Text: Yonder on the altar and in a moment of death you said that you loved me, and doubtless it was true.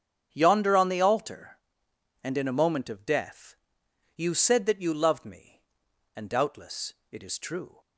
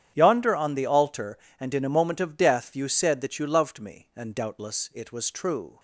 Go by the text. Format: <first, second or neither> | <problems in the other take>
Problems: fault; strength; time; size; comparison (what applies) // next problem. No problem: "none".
second | starts louder than the rest; strong; until 1.3 s; 8.5 dB; strong in the second // pauses between "death" and "you"; noticeable; at 3.5 s; 0.60 s long // pauses between "doubtless" and "it"; slight; at 6.9 s; 0.18 s long // says "is" for "was"; at 7.2 s